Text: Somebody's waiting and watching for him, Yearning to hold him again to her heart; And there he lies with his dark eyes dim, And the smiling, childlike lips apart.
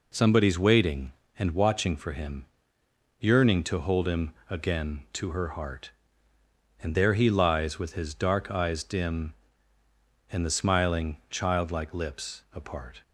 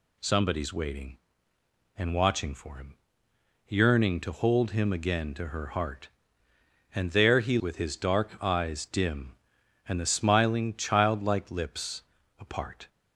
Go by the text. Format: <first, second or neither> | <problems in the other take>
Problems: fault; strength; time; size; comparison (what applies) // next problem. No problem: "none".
first | skips "lies"; at 7.5 s // pauses between "lips" and "apart"; slight; at 12.0 s; 0.36 s long